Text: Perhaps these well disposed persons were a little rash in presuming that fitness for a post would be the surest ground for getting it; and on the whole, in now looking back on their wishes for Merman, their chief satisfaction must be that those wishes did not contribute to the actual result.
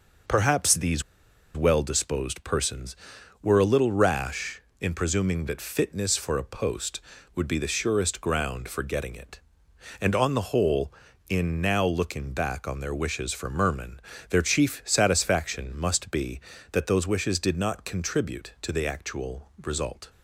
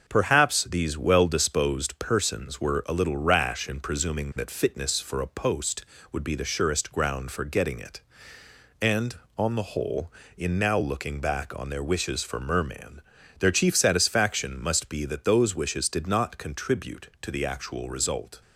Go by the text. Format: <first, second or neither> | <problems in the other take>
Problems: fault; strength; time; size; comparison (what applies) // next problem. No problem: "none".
second | pauses between "these" and "well"; noticeable; at 1.0 s; 0.53 s long